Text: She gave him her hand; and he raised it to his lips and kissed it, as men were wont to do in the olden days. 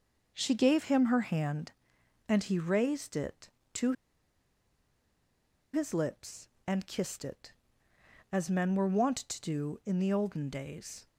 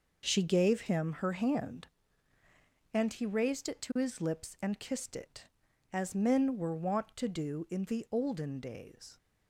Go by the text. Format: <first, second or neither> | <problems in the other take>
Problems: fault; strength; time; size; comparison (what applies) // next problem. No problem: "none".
second | pauses between "to" and "his"; strong; at 3.9 s; 1.8 s long